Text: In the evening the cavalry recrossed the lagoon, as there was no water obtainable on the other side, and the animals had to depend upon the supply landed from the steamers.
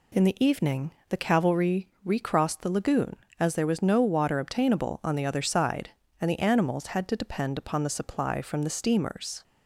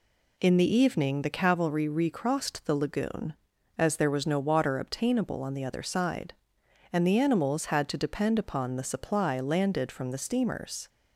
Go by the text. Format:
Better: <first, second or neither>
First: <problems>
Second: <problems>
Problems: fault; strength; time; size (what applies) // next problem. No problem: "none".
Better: second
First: pauses between "evening" and "the"; slight; at 0.9 s; 0.18 s long // pauses between "cavalry" and "recrossed"; slight; at 1.8 s; 0.18 s long // skips "landed"; at 8.4 s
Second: none